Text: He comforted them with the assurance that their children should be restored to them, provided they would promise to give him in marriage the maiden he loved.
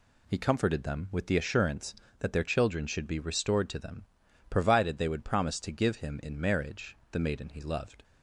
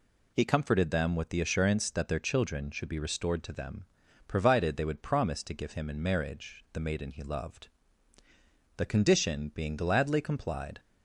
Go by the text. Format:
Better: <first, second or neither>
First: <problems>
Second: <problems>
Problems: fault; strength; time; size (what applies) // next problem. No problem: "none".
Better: first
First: none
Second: goes on to say "The condition being gladly complied"; strong; from 8.7 s on; 2.0 s long